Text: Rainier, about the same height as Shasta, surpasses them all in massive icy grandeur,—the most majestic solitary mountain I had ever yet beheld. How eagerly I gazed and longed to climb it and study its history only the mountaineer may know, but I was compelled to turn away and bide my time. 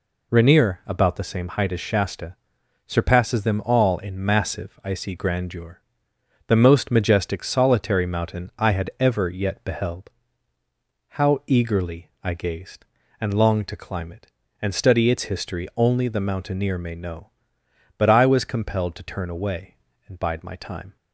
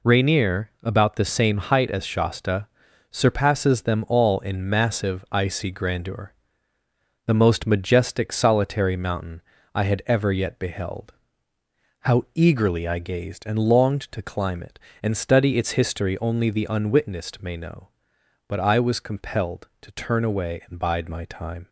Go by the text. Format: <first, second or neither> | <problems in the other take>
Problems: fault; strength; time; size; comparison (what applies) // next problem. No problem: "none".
first | pauses between "mountain" and "I"; slight; at 9.4 s; 0.32 s long // says "unwitnessed" for "mountaineer"; at 16.7 s